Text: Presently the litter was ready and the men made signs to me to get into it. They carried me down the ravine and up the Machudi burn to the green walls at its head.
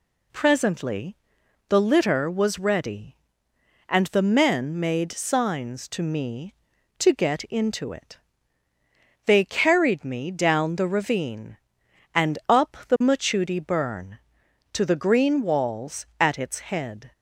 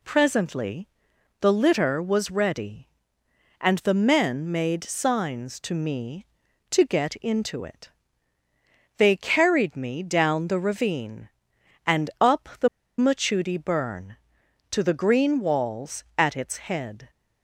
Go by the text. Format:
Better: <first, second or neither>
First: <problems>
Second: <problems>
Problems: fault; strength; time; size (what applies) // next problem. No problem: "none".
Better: first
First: pauses between "Presently" and "the"; noticeable; at 1.1 s; 0.52 s long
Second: pauses between "Presently" and "the"; noticeable; at 0.8 s; 0.52 s long // pauses between "the" and "Machudi"; slight; at 12.6 s; 0.30 s long